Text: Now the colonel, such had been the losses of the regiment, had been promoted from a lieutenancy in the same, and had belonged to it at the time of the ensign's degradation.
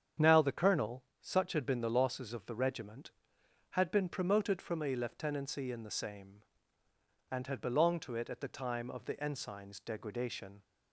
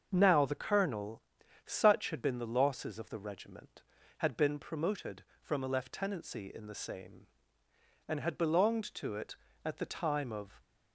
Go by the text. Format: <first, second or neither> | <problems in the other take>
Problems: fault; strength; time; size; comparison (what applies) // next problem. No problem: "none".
first | starts louder than the rest; until 1.1 s; 6.5 dB; strong in the first // stops before "the ensign's degradation"; at 10.6 s